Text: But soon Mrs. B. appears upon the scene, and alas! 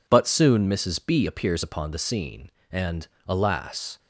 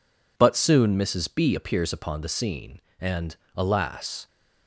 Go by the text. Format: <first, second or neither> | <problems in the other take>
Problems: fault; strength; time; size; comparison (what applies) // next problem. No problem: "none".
neither | pauses between "and" and "alas"; slight; the same in both